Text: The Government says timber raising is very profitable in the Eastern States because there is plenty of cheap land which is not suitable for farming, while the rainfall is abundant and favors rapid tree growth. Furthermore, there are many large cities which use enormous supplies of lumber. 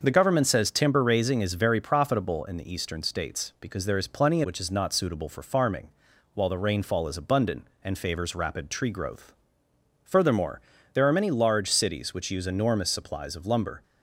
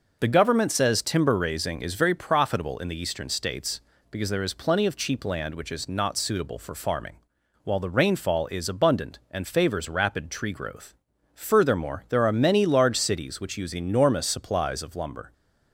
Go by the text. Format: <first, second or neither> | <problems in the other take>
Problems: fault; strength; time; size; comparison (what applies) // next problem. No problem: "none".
second | starts louder than the rest; until 1.0 s; 6 dB // skips "of cheap land"; at 4.4 s